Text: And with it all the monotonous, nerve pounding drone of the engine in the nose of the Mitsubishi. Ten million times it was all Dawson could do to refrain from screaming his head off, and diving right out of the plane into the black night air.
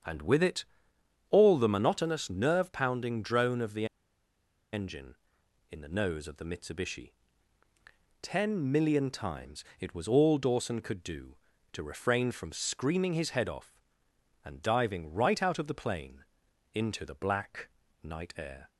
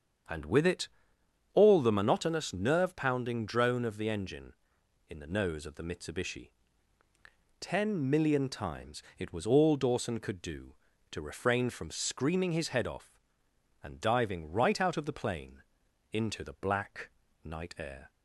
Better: second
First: starts louder than the rest; strong; until 1.6 s; 7.5 dB // pauses between "it" and "all"; noticeable; at 0.6 s; 0.64 s long // pauses between "the" and "engine"; noticeable; at 3.8 s; 0.87 s long // pauses between "times" and "it"; slight; at 9.6 s; 0.16 s long // pauses between "plane" and "into"; noticeable; at 16.2 s; 0.48 s long // pauses between "black" and "night"; slight; at 17.6 s; 0.34 s long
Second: starts louder than the rest; strong; until 1.9 s; 7.5 dB // pauses between "it" and "all"; noticeable; at 0.8 s; 0.64 s long // pauses between "times" and "it"; slight; at 9.0 s; 0.16 s long // pauses between "plane" and "into"; noticeable; at 15.6 s; 0.48 s long // pauses between "black" and "night"; slight; at 17.0 s; 0.34 s long

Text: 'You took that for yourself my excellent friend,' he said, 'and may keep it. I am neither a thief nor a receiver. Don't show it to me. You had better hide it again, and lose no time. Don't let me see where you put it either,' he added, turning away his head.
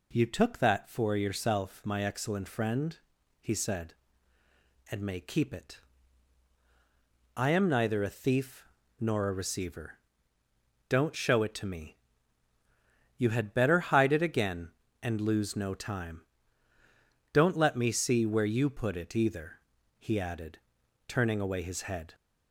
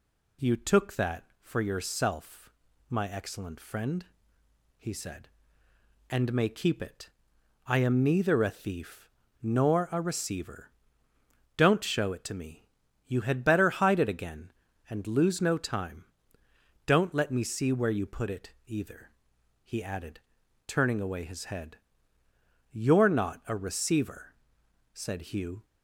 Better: first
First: pauses between "thief" and "nor"; slight; at 8.6 s; 0.34 s long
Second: pauses between "yourself" and "my"; at 2.5 s; 0.38 s long // pauses between "thief" and "nor"; slight; at 9.0 s; 0.32 s long // pauses between "it" and "either"; slight; at 18.5 s; 0.16 s long // goes on to say "You're not a receiver said Hugh"; strong; from 22.6 s on; 2.9 s long

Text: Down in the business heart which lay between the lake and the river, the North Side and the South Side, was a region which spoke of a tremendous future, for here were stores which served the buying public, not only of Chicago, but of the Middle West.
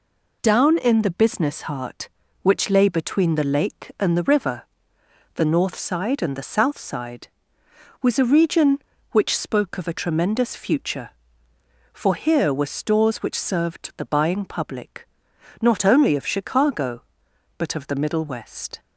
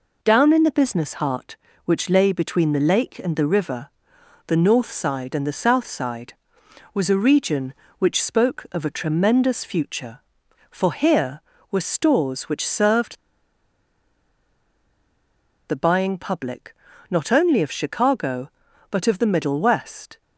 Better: first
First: none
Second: pauses between "served" and "the"; strong; at 13.1 s; 2.5 s long

